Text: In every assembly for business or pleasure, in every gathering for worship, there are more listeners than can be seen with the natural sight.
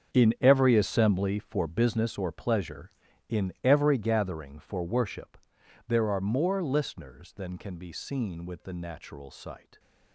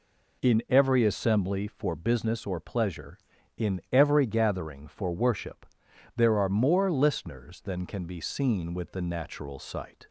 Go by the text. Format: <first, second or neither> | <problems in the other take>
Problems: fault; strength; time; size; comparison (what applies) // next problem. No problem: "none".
second | gets quieter; strong; throughout; 14 dB